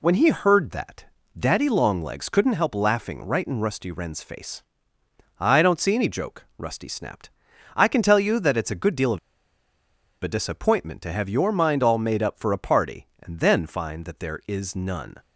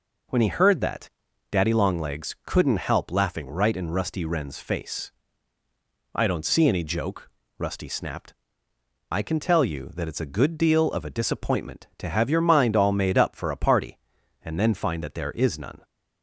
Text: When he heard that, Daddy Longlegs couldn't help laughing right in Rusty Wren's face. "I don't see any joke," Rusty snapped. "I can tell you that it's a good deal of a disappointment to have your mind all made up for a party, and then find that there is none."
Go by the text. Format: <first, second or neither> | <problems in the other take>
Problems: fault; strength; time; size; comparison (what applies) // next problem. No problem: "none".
second | pauses between "of" and "a"; at 9.1 s; 1.0 s long